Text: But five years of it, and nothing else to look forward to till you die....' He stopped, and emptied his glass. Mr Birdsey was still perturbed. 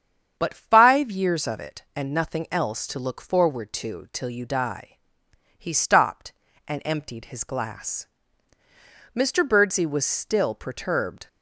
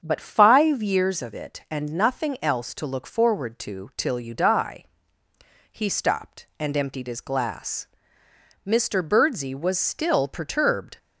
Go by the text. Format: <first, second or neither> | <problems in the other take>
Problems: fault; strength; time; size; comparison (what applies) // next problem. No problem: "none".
neither | starts louder than the rest; strong; the same in both